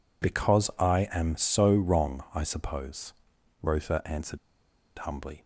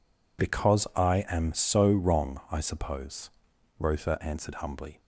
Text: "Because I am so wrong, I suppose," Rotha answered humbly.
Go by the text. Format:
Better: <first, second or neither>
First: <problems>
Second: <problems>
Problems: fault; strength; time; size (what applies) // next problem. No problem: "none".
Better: second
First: pauses between "answered" and "humbly"; noticeable; at 4.3 s; 0.67 s long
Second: none